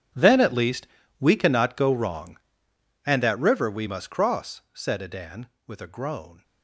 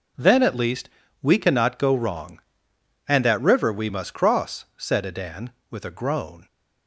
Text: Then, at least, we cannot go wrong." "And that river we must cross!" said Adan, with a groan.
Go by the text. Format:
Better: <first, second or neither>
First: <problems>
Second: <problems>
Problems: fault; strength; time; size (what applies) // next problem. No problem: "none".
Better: second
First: gets quieter; strong; throughout; 16 dB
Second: none